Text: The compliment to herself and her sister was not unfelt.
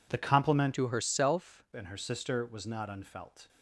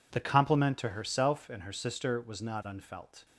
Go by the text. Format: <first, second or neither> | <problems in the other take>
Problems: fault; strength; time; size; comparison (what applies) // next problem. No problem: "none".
second | changes voice from "to" to "herself"; from 0.7 to 1.6 s; 0.9 s long